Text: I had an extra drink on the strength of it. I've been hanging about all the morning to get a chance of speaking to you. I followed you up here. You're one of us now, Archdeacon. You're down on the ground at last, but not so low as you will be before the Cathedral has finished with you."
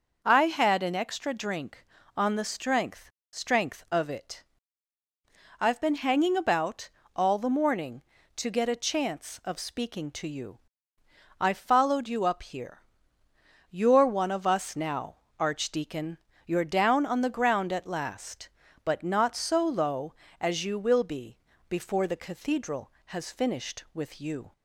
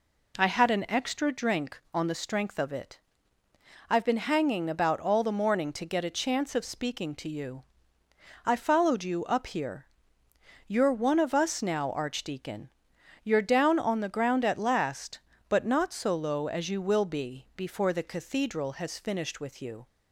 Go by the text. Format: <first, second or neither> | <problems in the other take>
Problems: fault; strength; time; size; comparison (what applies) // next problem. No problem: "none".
second | says "strength" twice; at 3.3 s // pauses between "about" and "all"; slight; at 6.9 s; 0.26 s long // pauses between "be" and "before"; slight; at 21.3 s; 0.32 s long